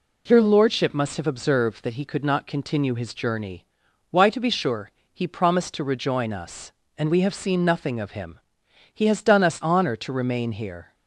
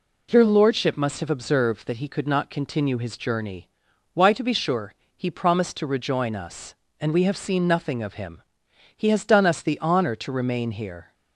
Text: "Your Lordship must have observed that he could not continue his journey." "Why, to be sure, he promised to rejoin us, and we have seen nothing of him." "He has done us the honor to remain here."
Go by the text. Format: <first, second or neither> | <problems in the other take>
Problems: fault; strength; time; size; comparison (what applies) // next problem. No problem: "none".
second | skips "the"; at 9.6 s